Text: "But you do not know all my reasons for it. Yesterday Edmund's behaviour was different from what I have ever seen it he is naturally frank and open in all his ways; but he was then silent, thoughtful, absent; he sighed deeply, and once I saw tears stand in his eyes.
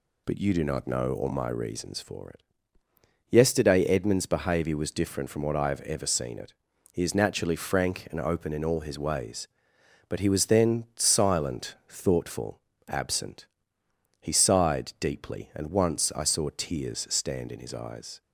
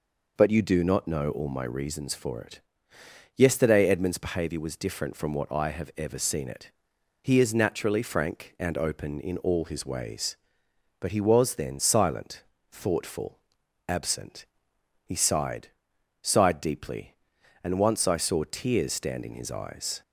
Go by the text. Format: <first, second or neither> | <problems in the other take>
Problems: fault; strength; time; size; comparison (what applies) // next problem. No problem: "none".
first | pauses between "it" and "he"; noticeable; at 6.7 s; 0.50 s long; also in the first // says "sighed" twice; at 16.2 s